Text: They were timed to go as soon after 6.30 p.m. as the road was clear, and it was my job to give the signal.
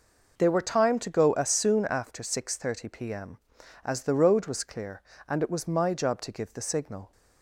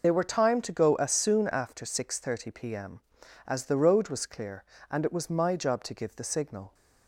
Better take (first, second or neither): first